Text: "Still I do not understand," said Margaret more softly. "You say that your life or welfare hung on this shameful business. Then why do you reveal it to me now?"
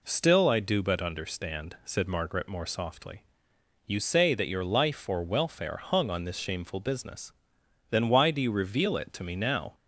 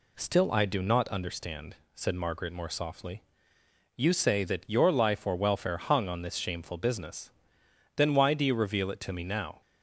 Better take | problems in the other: second | says "but" for "not"; at 0.8 s

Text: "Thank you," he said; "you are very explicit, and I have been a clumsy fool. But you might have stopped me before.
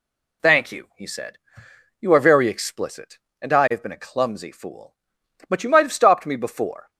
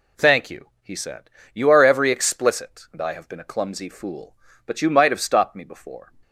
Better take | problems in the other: first | says "every" for "very"; at 1.8 s

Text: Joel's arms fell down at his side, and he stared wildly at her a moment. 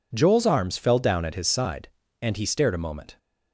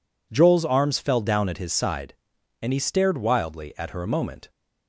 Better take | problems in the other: second | skips "wildly at her"; at 2.7 s

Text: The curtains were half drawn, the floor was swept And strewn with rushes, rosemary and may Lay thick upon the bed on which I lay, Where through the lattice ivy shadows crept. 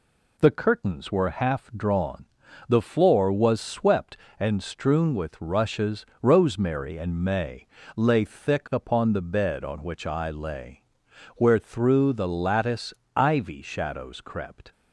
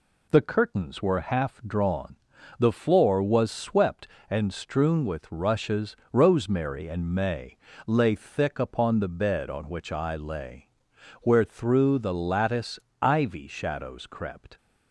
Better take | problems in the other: neither | pauses between "may" and "Lay"; slight; the same in both // pauses between "lattice" and "ivy"; slight; the same in both

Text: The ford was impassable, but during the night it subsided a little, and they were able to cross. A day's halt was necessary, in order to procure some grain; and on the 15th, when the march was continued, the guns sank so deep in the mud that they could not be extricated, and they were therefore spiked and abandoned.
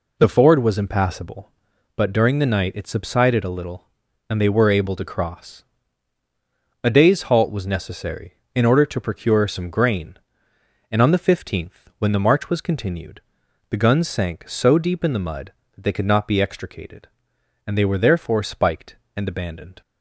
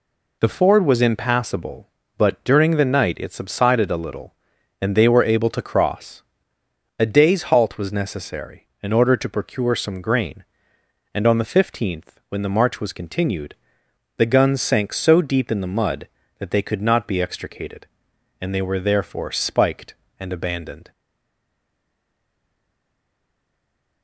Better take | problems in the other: first | stays silent after the last word; strong; from 20.9 s on; 3.1 s long

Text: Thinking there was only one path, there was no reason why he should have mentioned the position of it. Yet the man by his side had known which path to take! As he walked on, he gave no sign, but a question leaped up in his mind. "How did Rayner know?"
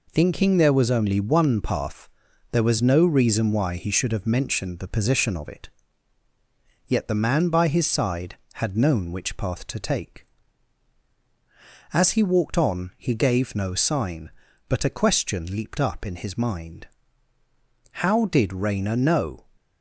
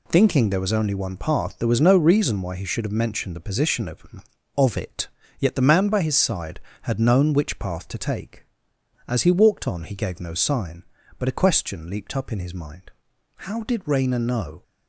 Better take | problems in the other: first | says "of" twice; at 4.5 s

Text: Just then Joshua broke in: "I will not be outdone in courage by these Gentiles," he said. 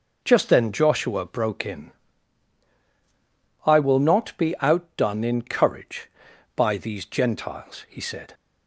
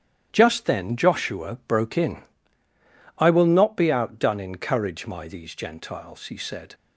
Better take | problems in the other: first | starts louder than the rest; strong; until 1.3 s; 11 dB // says "my" for "by"; at 5.0 s

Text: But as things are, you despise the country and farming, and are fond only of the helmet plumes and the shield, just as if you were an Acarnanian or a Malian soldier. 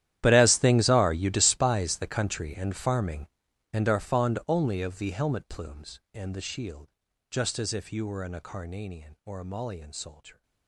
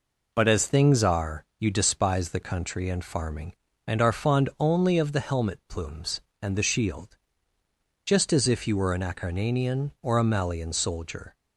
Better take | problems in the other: second | gets quieter; strong; throughout; 20 dB

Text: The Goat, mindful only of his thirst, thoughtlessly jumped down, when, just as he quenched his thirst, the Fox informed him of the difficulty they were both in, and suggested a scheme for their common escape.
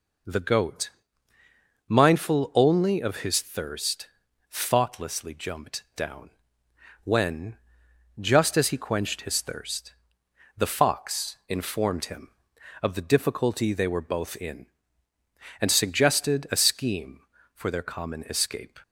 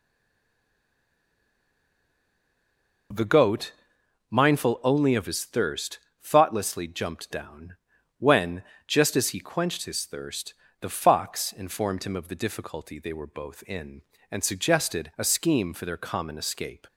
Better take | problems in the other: first | stays silent before the first word; strong; until 3.1 s; 3.1 s long

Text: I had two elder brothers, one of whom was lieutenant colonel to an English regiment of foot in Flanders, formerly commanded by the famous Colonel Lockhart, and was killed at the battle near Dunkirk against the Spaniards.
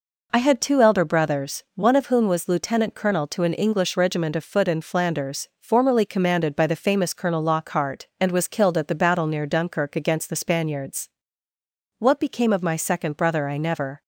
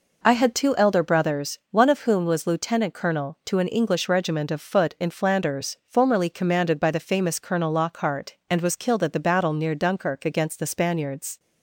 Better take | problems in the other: second | goes on to say "What became of my second brother I never"; strong; from 11.9 s on; 2.0 s long

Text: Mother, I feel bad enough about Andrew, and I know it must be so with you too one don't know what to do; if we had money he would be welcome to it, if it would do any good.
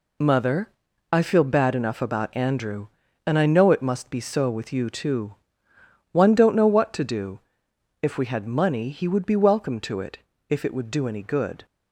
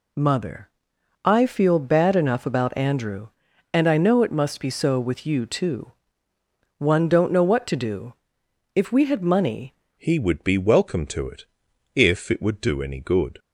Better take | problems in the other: first | pauses between "too" and "one"; noticeable; at 5.9 s; 0.86 s long; noticeable in the first // changes voice at "he"; from 9.9 s on; 3.4 s long

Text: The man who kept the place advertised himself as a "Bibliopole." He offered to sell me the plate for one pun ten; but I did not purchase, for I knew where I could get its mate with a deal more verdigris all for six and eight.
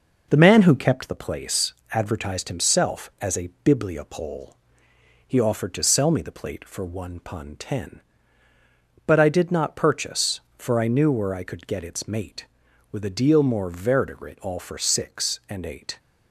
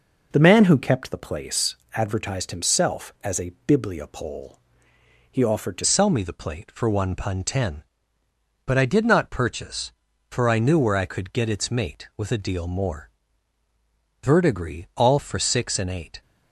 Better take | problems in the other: first | pauses between "place" and "advertised"; slight; at 1.7 s; 0.18 s long; slight in the first // pauses between "a" and "Bibliopole"; slight; at 3.5 s; 0.16 s long; slight in the first // changes voice at "sell"; from 5.8 s on; 10.4 s long // pauses between "more" and "verdigris"; at 13.0 s; 1.1 s long

